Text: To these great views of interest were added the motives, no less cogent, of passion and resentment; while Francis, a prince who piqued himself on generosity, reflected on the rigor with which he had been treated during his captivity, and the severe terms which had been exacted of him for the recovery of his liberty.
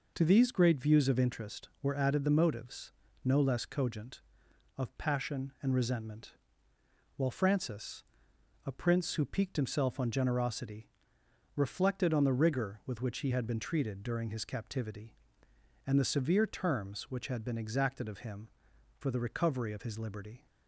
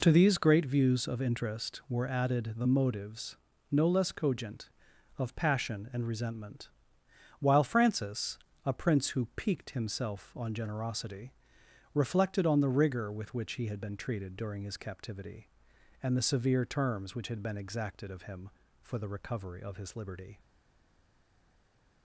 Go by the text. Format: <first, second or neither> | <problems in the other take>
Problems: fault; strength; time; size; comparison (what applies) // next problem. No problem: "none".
first | stays silent after the last word; noticeable; from 20.3 s on; 1.7 s long